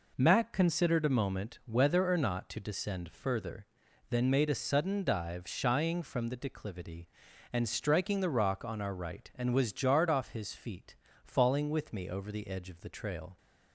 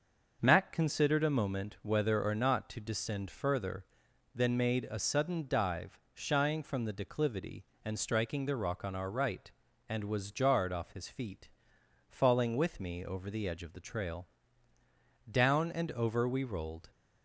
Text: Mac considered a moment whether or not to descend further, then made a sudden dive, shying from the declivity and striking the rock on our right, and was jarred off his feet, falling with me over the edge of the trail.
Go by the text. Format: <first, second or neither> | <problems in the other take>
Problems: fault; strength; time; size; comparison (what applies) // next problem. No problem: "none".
first | starts louder than the rest; noticeable; until 1.4 s; 6 dB // goes on to say "Down and over we rolled"; from 15.2 s on; 1.6 s long